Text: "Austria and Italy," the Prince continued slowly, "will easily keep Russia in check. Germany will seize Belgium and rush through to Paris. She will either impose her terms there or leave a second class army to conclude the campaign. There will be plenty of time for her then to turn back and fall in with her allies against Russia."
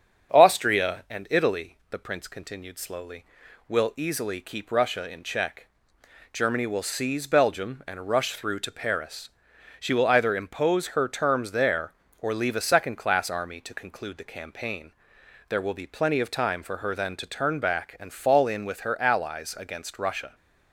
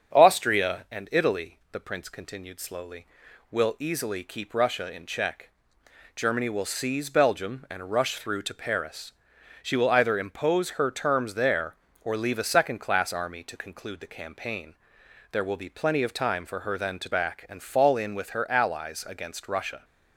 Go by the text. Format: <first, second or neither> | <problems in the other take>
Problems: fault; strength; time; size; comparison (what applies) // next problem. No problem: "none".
first | starts louder than the rest; strong; until 1.2 s; 7 dB; strong in the first // skips "turn"; at 17.1 s